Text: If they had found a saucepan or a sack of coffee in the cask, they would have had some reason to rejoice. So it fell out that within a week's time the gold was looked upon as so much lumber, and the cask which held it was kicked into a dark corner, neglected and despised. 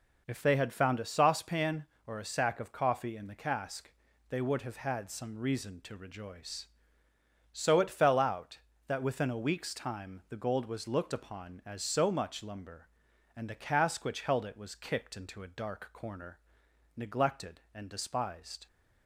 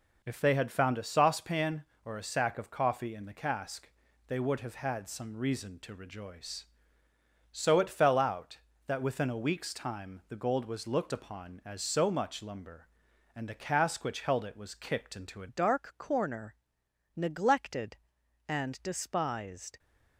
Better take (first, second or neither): first